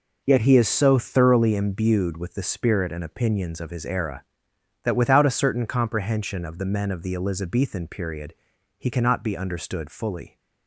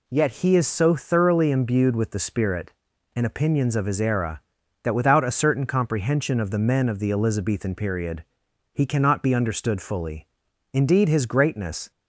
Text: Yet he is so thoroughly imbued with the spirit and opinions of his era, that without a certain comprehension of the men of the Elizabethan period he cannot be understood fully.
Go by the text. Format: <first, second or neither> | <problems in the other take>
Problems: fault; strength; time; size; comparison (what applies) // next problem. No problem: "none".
first | pauses between "period" and "he"; noticeable; at 8.2 s; 0.50 s long; also in the first // goes on to say "Indeed his greatness"; noticeable; from 10.7 s on; 1.1 s long